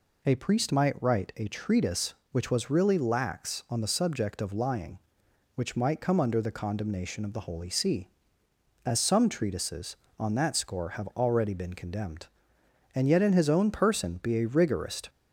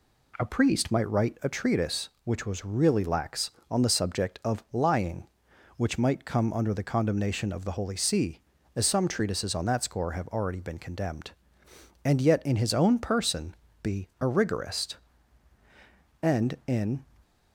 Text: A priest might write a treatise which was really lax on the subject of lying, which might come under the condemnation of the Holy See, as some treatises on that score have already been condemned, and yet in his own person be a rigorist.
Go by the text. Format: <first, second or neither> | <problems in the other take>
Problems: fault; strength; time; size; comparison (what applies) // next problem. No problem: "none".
first | pauses between "person" and "be"; slight; at 13.5 s; 0.28 s long // goes on to say "And in"; noticeable; from 16.2 s on; 0.82 s long